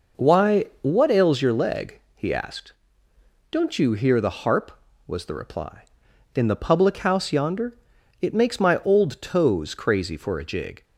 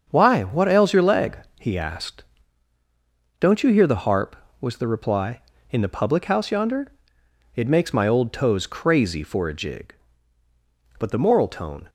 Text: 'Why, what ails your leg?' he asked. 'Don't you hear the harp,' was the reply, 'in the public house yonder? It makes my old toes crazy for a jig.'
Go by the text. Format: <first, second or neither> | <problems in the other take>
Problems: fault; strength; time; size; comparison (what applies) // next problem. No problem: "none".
first | starts louder than the rest; until 1.1 s; 7 dB // goes on to say "But the moral tone"; noticeable; from 10.9 s on; 0.90 s long